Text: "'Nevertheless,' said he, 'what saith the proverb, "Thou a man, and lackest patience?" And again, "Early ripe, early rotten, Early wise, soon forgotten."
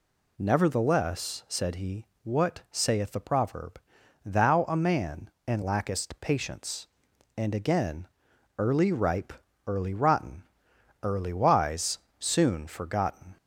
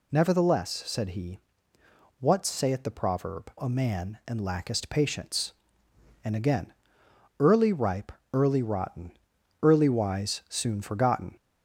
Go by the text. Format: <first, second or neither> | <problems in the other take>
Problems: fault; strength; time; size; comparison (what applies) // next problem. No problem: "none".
first | skips "Thou"; at 3.5 s